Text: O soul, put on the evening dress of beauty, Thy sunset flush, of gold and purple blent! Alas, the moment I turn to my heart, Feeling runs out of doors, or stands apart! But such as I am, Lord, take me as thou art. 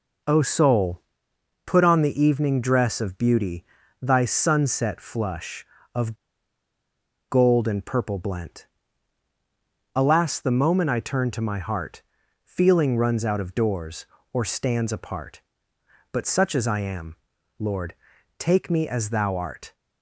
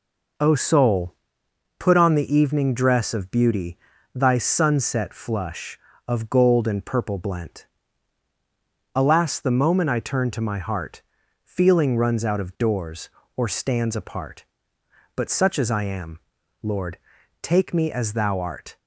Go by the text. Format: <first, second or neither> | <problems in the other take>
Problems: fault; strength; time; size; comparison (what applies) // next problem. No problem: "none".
second | pauses between "of" and "gold"; at 6.1 s; 1.1 s long